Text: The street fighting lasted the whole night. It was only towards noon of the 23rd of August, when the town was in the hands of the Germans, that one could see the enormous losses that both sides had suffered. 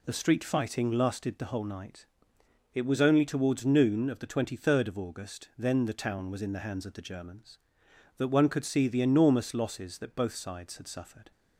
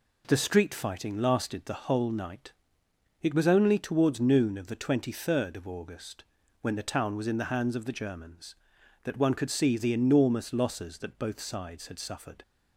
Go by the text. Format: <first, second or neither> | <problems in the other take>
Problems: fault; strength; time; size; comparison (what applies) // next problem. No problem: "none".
second | says "then" for "when"; at 5.5 s